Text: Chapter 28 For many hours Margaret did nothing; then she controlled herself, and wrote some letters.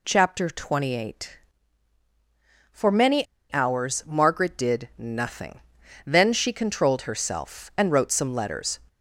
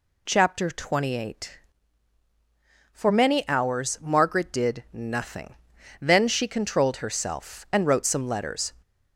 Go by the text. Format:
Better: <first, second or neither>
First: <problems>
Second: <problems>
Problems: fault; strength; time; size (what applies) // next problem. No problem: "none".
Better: second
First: pauses between "many" and "hours"; slight; at 3.2 s; 0.24 s long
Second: none